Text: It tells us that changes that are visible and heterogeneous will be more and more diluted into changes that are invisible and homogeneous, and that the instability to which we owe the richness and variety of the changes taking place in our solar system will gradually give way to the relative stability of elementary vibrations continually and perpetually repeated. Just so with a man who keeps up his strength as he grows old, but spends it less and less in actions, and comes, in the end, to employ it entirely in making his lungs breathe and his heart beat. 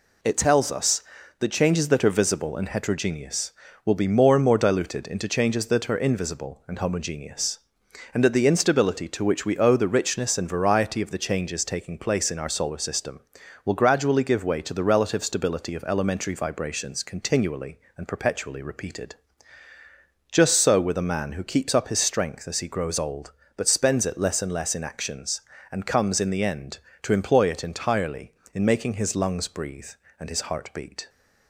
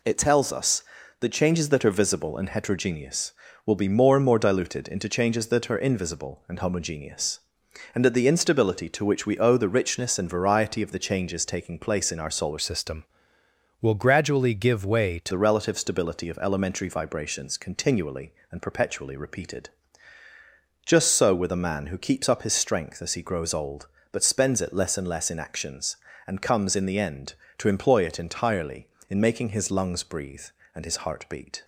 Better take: first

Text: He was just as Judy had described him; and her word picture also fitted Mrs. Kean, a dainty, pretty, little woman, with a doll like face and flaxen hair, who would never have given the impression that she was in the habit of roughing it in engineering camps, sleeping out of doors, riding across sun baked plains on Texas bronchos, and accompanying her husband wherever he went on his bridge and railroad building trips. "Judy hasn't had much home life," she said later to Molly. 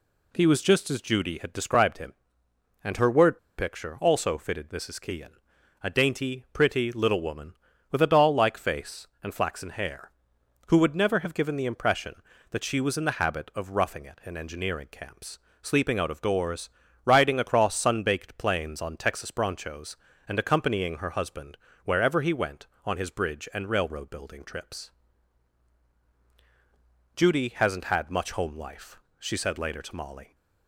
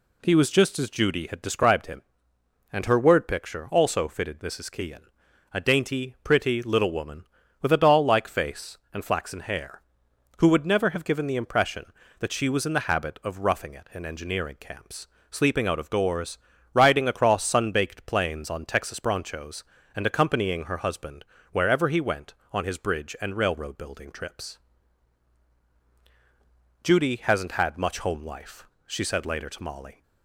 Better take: second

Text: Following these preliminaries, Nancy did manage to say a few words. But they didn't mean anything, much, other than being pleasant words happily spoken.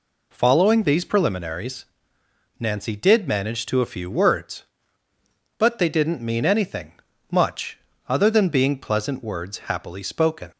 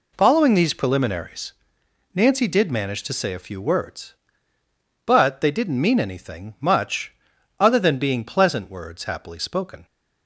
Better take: second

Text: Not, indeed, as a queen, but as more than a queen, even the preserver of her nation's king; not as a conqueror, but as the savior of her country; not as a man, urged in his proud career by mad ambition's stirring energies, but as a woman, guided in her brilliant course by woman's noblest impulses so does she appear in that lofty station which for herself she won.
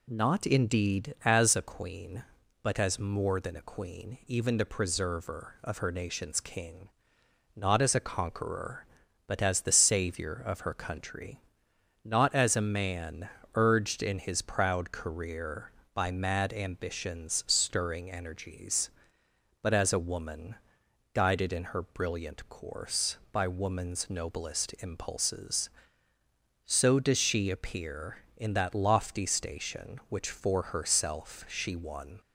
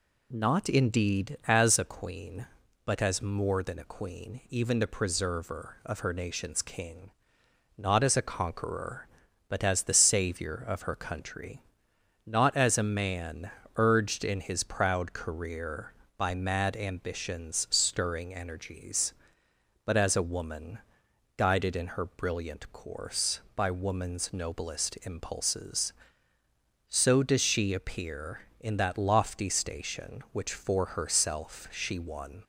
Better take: neither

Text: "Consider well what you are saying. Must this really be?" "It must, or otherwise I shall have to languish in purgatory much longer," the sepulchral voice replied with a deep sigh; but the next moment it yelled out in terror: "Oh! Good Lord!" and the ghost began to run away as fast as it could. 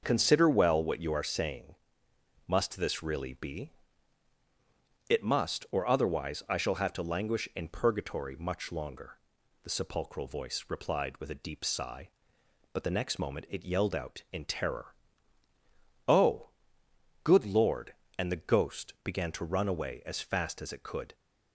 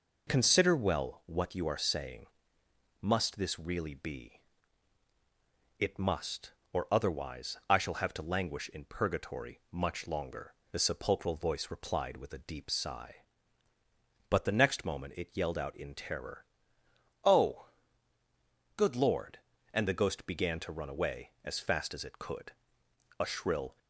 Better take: first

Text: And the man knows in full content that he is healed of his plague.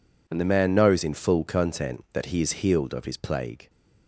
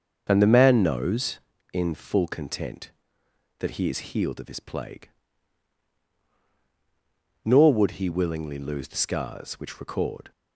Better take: first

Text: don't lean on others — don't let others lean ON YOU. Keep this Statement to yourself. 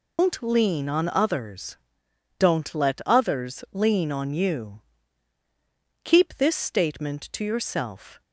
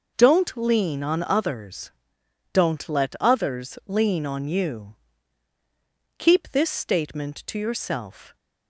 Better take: second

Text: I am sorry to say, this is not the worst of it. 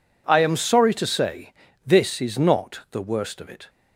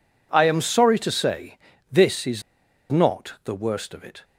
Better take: first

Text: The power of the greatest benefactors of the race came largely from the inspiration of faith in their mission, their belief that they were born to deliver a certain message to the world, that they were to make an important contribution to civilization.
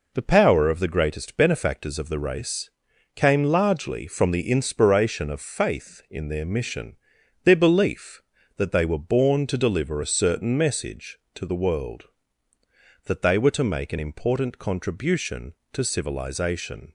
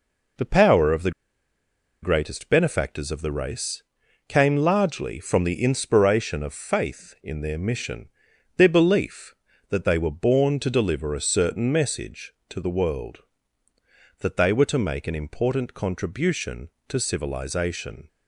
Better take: first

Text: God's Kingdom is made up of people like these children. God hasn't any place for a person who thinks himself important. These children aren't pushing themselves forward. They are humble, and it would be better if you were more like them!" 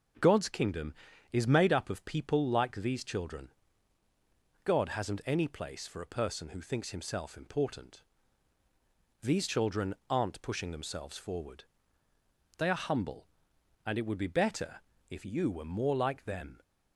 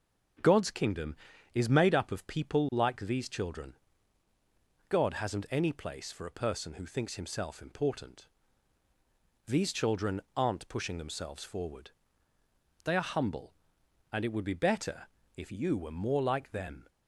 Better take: neither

